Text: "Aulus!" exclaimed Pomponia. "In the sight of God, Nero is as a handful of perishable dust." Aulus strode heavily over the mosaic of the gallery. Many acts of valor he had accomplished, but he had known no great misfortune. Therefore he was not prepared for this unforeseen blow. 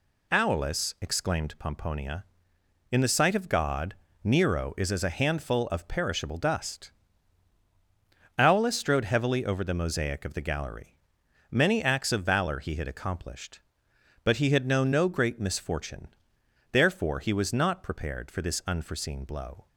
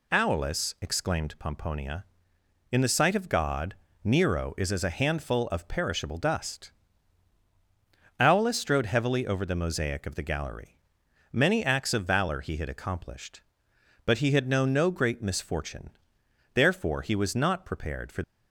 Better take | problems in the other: first | stops before "this unforeseen blow"; at 18.2 s

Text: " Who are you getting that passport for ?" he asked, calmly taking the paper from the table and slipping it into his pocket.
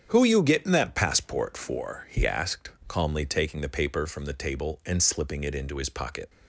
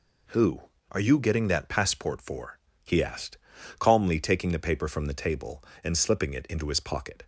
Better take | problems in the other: second | starts louder than the rest; strong; until 1.0 s; 8 dB // skips "are"; at 0.2 s

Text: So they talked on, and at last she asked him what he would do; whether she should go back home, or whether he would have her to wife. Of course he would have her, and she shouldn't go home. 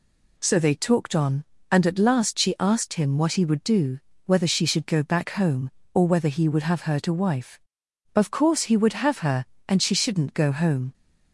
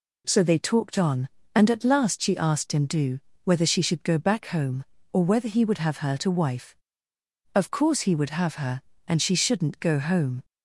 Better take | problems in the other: first | skips "what he would"; at 2.8 s

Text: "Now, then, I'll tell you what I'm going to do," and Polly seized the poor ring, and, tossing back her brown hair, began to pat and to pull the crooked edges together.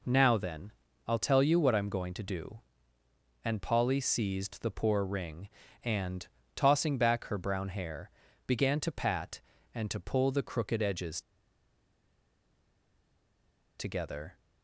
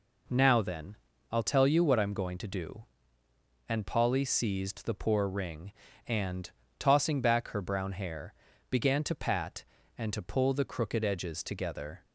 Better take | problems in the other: second | pauses between "edges" and "together"; strong; at 11.2 s; 2.5 s long

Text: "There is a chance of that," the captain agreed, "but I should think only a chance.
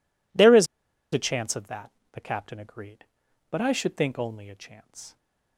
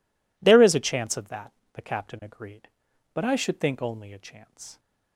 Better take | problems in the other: second | pauses between "is" and "a"; noticeable; at 0.6 s; 0.47 s long

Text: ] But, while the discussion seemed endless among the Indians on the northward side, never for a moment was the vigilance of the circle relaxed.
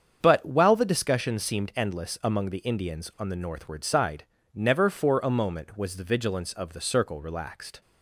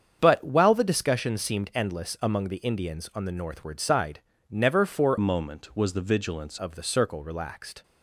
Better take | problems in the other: first | starts louder than the rest; strong; until 1.2 s; 7.5 dB; strong in the first // changes voice from "a" to "vigilance"; from 5.1 to 6.5 s; 1.4 s long

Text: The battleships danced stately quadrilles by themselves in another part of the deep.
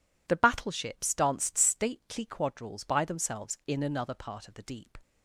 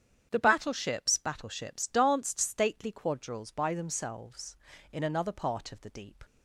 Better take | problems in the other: first | starts louder than the rest; strong; until 1.3 s; 9 dB // says "battleships" twice; at 1.1 s

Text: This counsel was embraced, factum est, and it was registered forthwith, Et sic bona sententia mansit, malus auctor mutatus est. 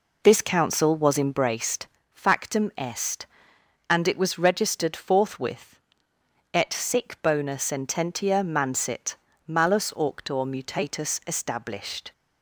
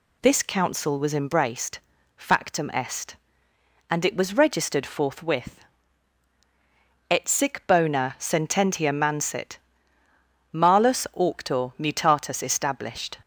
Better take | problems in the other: second | starts louder than the rest; noticeable; until 1.9 s; 4 dB

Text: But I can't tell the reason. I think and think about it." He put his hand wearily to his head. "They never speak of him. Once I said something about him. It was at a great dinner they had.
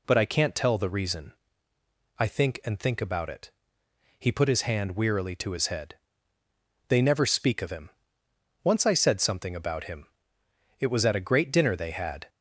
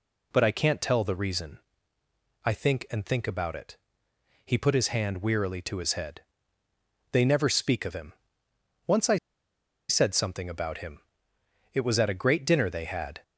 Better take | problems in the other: first | pauses between "I" and "said"; noticeable; at 9.1 s; 0.71 s long

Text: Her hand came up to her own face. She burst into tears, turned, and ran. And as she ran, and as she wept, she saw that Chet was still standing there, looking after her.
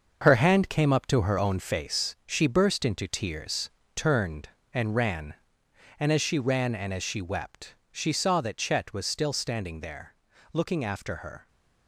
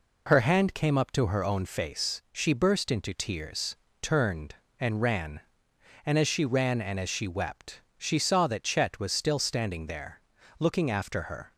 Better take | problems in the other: second | gets quieter; strong; throughout; 8 dB

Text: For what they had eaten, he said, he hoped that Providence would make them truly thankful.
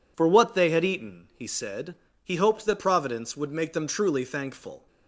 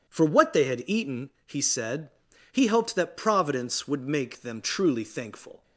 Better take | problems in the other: neither | none

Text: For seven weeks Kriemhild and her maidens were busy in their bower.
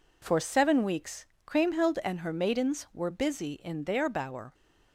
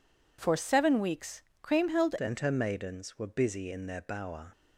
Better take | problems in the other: first | pauses between "weeks" and "Kriemhild"; slight; at 1.4 s; 0.20 s long; slight in the first // changes voice at "and"; from 2.1 s on; 2.4 s long

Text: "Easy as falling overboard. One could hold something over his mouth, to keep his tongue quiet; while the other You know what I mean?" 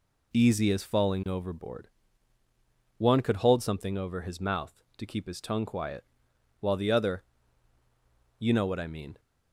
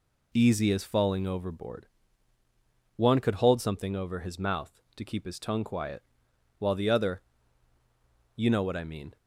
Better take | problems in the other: neither | pauses between "other" and "You"; the same in both

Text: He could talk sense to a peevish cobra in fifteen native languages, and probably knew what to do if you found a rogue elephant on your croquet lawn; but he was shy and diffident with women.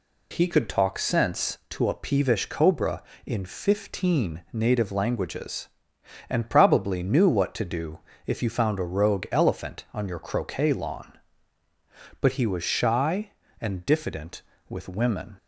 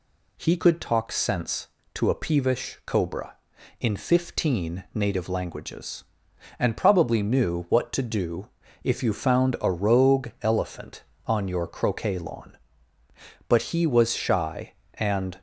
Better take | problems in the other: first | pauses between "do" and "if"; slight; at 8.4 s; 0.34 s long; slight in the first // stops before "diffident with women"; at 15.3 s

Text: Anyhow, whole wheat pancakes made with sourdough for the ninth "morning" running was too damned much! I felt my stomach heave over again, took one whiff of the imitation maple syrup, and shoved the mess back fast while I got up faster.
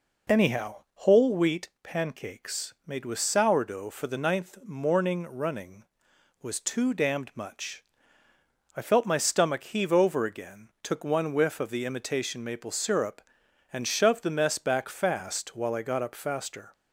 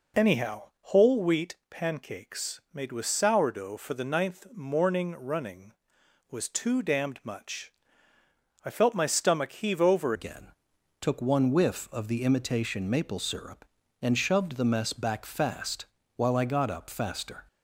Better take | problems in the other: first | changes voice at "again"; from 10.1 s on; 7.3 s long // pauses between "fast" and "while"; slight; at 15.8 s; 0.28 s long

